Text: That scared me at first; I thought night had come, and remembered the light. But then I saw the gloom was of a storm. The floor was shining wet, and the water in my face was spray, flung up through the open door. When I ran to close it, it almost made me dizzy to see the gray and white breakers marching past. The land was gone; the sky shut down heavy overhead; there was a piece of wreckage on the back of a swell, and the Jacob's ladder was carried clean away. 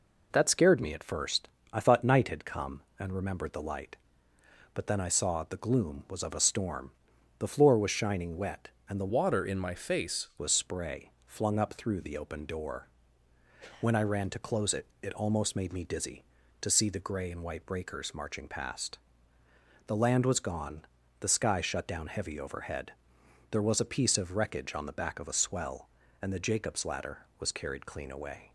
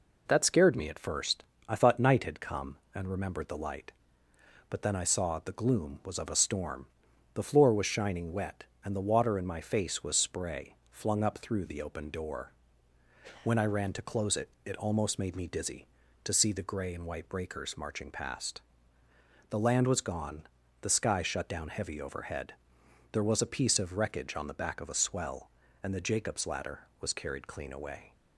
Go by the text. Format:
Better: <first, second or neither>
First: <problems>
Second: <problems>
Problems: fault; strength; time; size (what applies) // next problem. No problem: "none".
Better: second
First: changes voice from "water" to "face"; from 9.1 to 10.2 s; 1.1 s long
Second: none